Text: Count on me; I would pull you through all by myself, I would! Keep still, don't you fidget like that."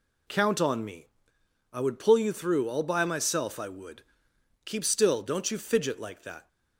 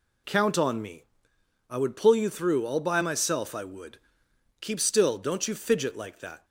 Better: neither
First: none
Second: none

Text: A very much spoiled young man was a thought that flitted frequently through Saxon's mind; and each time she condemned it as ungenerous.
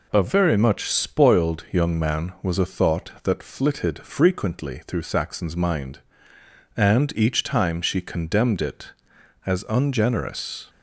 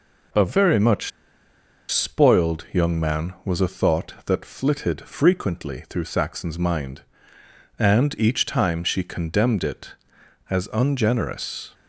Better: first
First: none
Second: pauses between "much" and "spoiled"; noticeable; at 1.1 s; 0.80 s long

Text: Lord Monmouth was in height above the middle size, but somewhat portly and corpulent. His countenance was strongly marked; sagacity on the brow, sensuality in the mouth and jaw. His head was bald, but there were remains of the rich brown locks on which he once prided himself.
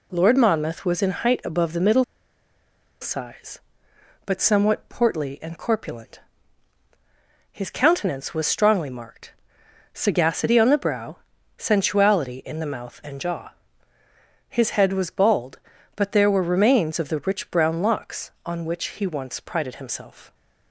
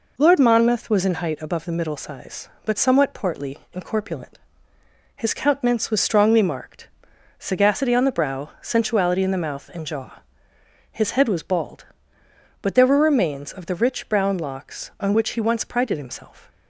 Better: second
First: pauses between "middle" and "size"; at 2.0 s; 0.98 s long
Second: none

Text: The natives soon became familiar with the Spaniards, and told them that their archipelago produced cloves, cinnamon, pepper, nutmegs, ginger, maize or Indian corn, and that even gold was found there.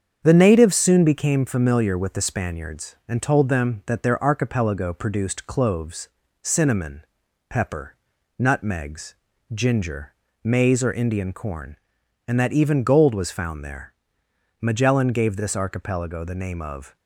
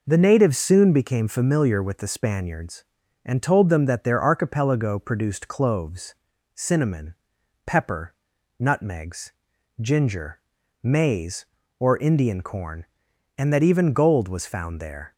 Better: second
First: starts louder than the rest; strong; until 1.2 s; 7.5 dB // goes on to say "Magellan gave this archipelago the name of"; strong; from 14.5 s on; 2.3 s long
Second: none

